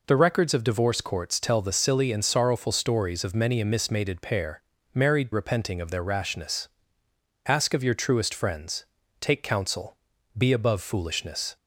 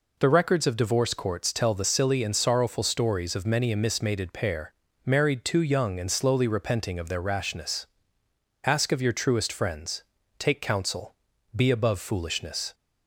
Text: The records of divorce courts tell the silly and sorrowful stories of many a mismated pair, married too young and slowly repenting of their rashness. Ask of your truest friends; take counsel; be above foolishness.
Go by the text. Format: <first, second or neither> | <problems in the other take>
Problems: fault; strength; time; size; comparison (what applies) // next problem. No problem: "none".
second | skips "too young and slowly"; at 5.3 s